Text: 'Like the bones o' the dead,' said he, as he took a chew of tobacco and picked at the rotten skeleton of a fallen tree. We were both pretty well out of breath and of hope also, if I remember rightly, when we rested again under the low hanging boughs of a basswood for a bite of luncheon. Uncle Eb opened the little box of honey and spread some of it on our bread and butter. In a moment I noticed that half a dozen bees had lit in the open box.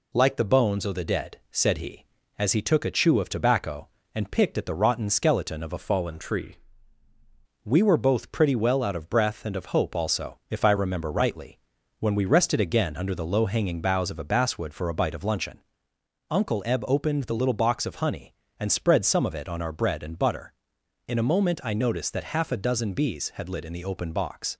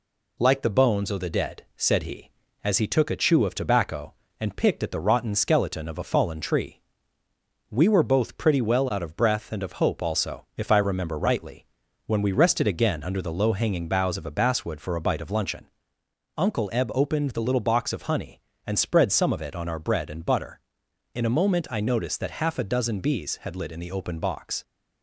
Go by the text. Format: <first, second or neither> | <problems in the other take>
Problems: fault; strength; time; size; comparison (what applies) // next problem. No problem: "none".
second | changes voice from "fallen" to "tree"; from 5.7 to 6.5 s; 0.8 s long